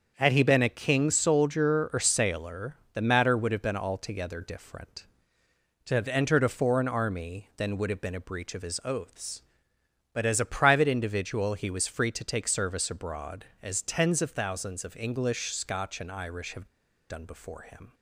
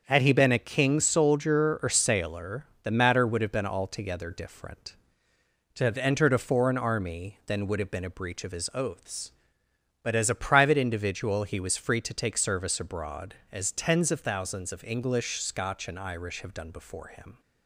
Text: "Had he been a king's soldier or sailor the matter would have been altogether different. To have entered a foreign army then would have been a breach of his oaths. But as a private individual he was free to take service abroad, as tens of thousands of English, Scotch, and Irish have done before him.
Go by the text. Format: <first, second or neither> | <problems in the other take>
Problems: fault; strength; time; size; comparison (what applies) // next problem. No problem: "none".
second | starts louder than the rest; until 1.1 s; 7 dB; also in the second // pauses between "sailor" and "the"; slight; at 2.7 s; 0.18 s long; slight in the second // pauses between "have" and "done"; at 16.6 s; 0.43 s long